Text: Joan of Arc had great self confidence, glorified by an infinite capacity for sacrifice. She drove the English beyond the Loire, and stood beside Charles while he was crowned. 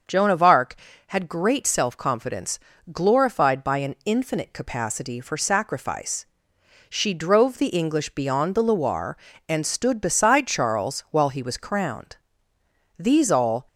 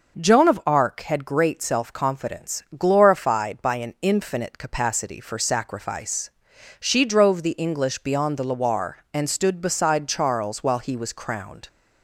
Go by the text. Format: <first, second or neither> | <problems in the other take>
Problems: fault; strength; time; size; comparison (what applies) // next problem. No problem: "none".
second | starts louder than the rest; until 1.3 s; 6.5 dB // goes on to say "These all"; noticeable; from 12.9 s on; 0.70 s long